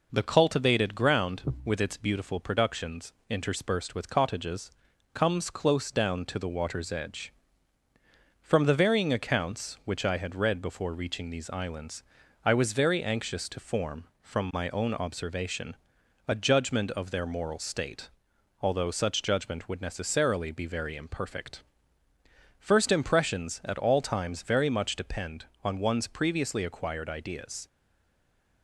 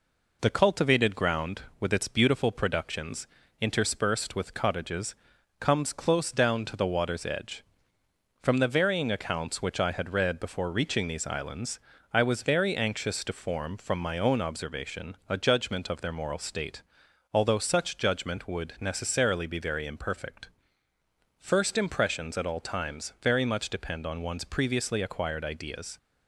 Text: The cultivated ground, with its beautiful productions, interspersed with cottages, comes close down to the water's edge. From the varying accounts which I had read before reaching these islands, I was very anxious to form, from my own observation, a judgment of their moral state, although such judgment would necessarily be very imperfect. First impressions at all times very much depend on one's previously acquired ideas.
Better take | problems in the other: second | stays silent after the last word; from 27.6 s on; 1.0 s long

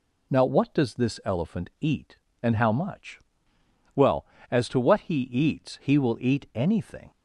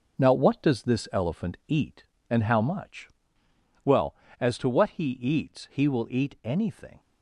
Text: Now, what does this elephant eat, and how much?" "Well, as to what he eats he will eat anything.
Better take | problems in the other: first | gets quieter; strong; throughout; 8 dB

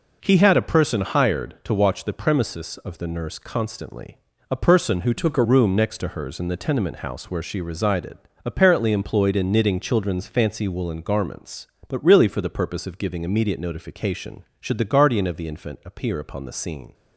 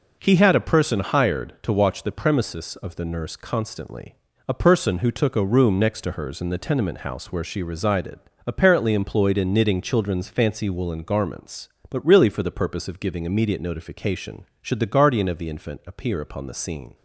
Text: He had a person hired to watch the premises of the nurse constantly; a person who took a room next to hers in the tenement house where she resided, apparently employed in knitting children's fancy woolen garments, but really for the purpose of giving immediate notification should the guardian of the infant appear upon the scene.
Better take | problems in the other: second | changes voice from "took" to "a"; from 5.1 to 5.4 s; 0.3 s long

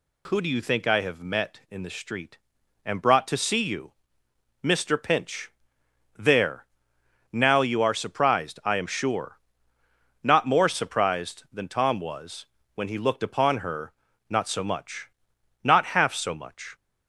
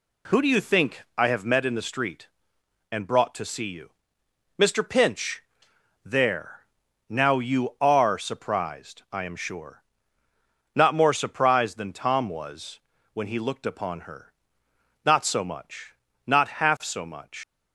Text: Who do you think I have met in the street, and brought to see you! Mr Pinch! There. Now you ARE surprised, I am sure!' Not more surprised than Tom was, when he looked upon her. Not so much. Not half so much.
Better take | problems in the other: first | leaves "much" unfinished; at 17.4 s; 115 ms

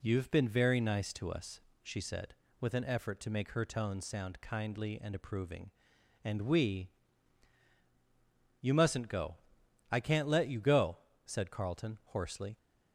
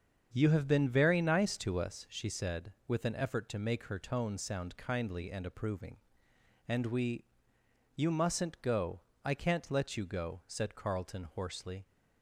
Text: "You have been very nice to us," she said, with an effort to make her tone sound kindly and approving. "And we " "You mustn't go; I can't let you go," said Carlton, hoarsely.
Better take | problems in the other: first | starts louder than the rest; strong; until 2.1 s; 7.5 dB

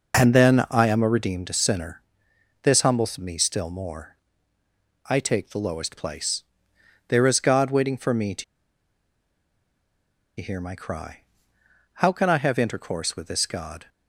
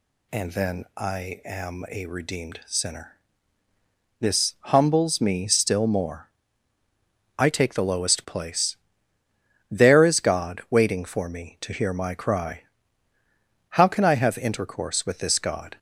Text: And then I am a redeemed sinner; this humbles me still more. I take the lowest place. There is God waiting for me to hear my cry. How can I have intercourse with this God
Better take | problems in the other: second | pauses between "to" and "hear"; strong; at 8.4 s; 1.9 s long

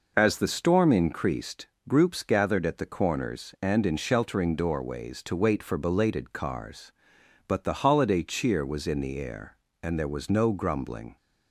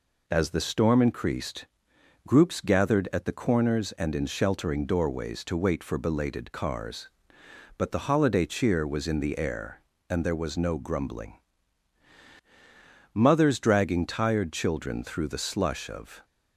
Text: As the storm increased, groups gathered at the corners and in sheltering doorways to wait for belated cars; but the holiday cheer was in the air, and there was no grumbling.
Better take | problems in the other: first | goes on to say "Mothers dragging tired children through the slush of"; strong; from 13.1 s on; 3.1 s long

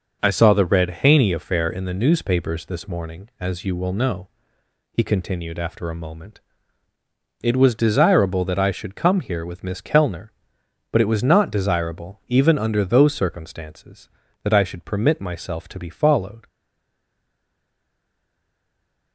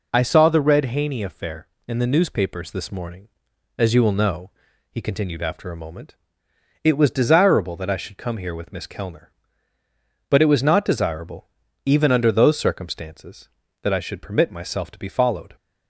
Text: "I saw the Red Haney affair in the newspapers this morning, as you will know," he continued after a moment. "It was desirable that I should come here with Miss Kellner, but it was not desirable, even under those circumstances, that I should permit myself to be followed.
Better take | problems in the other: second | stays silent after the last word; strong; from 16.4 s on; 2.7 s long

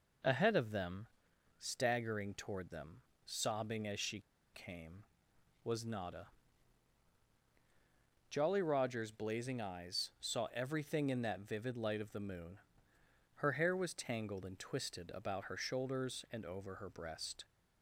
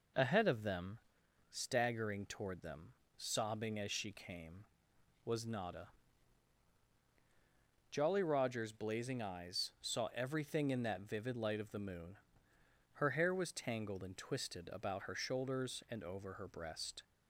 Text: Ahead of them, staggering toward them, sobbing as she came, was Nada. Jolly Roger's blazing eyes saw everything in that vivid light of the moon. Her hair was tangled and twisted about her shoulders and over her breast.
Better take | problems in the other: second | pauses between "she" and "came"; slight; at 4.2 s; 0.33 s long

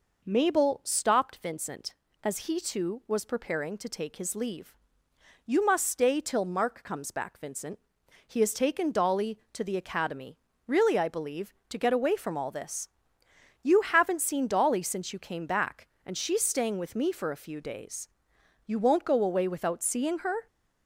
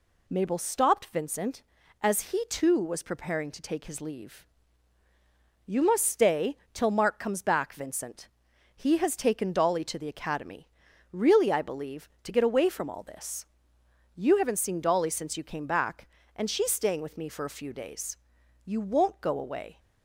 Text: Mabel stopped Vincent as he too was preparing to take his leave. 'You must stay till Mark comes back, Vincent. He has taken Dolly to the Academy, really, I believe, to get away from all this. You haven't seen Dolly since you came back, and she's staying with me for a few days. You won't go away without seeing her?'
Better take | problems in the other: first | pauses between "stay" and "till"; slight; at 6.5 s; 0.16 s long // stops before "without seeing her"; at 19.7 s

